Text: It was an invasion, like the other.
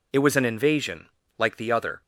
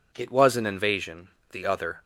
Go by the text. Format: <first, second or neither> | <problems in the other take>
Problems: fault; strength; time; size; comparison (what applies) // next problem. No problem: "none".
first | skips "like"; at 1.4 s